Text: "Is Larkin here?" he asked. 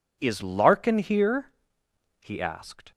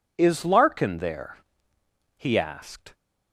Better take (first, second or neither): first